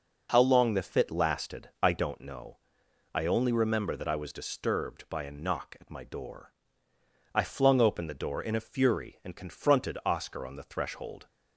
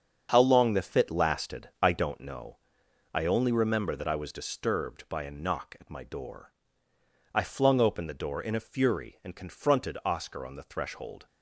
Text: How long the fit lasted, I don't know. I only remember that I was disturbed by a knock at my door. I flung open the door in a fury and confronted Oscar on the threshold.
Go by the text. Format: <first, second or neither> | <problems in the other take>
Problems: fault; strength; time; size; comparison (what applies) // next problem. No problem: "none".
first | gets quieter; strong; throughout; 8.5 dB